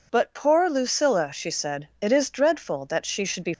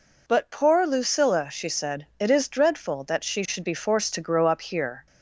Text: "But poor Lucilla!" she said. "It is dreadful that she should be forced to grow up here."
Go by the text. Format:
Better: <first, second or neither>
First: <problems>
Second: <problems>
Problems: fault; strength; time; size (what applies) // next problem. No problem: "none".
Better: second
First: stops before "forced to grow up here"; at 3.5 s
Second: none